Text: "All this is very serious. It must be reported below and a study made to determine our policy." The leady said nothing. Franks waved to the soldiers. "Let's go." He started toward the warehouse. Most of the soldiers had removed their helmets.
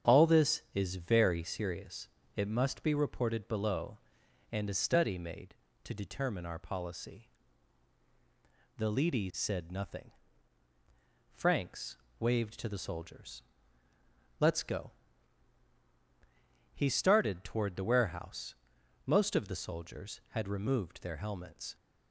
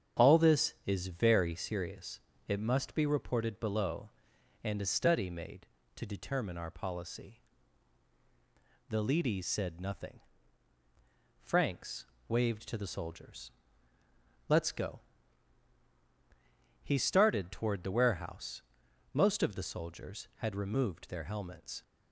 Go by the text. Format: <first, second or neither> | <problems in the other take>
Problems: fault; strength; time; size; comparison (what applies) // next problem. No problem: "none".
neither | starts louder than the rest; strong; the same in both // pauses between "Franks" and "waved"; slight; the same in both